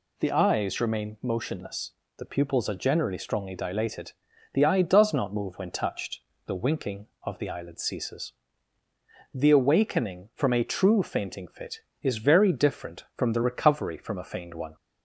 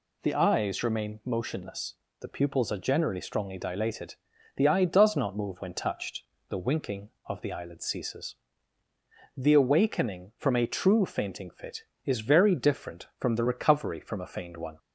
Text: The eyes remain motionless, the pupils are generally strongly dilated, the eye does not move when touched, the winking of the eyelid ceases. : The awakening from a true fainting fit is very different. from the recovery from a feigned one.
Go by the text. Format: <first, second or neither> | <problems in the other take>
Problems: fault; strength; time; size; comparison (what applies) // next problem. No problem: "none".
neither | none